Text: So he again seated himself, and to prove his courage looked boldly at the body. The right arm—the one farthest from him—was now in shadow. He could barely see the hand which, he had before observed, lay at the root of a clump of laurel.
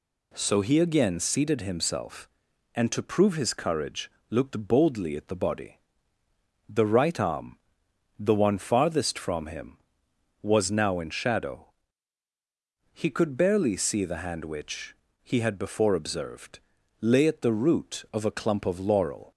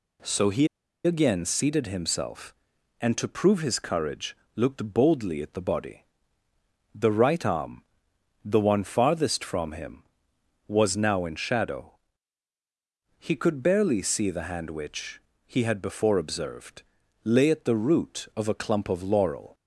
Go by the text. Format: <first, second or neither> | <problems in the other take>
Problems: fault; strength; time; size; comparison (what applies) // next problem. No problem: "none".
first | pauses between "he" and "again"; at 0.6 s; 0.37 s long // pauses between "courage" and "looked"; slight; at 4.3 s; 0.20 s long; slight in the first